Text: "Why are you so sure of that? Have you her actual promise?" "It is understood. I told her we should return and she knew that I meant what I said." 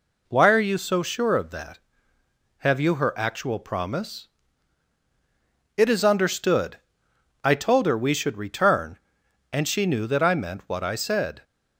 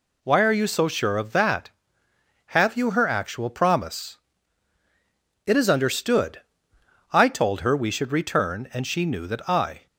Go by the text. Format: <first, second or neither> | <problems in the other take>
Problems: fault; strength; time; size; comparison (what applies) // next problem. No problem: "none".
first | stops before "meant what I said"; at 9.8 s